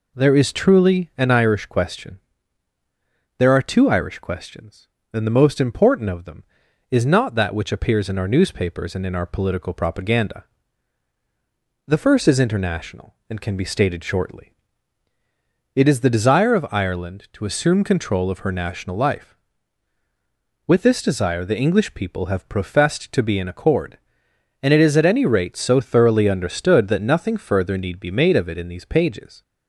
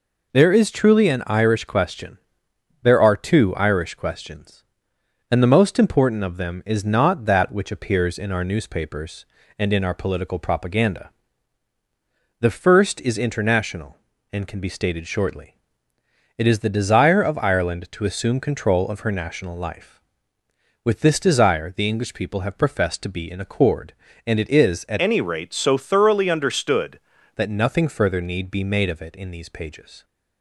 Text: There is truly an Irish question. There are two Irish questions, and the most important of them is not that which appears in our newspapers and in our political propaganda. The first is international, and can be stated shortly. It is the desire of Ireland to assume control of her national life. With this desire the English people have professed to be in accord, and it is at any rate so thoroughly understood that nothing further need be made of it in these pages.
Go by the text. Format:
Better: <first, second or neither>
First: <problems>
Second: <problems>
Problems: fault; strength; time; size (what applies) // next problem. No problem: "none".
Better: first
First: none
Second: changes voice from "any" to "understood"; from 24.9 to 26.9 s; 2.0 s long